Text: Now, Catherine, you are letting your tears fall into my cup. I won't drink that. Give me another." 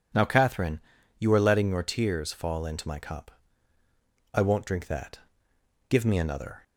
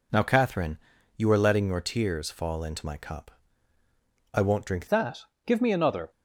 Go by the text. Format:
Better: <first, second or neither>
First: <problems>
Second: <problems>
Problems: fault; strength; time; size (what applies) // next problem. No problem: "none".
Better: first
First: none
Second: changes voice at "that"; from 4.8 s on; 1.3 s long